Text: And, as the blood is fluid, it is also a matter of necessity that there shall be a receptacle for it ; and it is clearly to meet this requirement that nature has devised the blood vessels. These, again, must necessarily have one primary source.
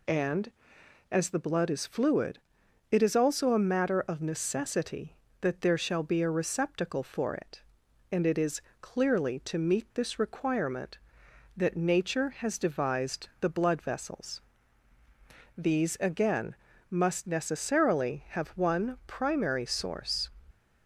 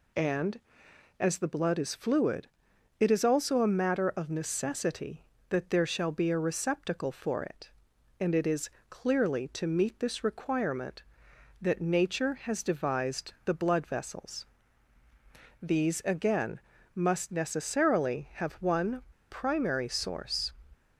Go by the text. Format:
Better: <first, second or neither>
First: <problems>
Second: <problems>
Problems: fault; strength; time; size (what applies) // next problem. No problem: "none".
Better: first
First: pauses between "is" and "clearly"; slight; at 8.5 s; 0.22 s long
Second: pauses between "is" and "clearly"; slight; at 8.6 s; 0.22 s long // pauses between "one" and "primary"; slight; at 19.0 s; 0.30 s long